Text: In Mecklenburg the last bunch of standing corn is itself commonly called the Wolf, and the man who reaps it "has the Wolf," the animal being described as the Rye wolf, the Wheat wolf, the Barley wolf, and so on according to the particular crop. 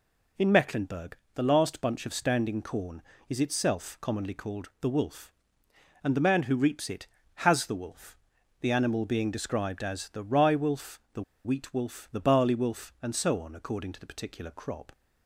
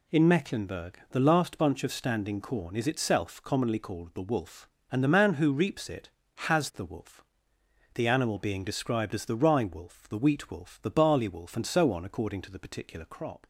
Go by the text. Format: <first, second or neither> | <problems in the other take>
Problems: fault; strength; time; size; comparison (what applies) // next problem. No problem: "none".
second | pauses between "Mecklenburg" and "the"; slight; at 1.1 s; 0.20 s long // pauses between "the" and "Wheat"; slight; at 11.2 s; 0.23 s long